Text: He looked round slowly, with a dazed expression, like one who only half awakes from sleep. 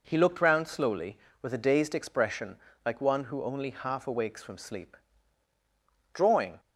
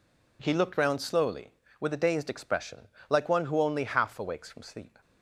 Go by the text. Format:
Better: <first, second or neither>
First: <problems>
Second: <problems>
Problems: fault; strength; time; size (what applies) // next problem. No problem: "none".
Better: second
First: goes on to say "Drawing"; slight; from 6.1 s on; 0.46 s long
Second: none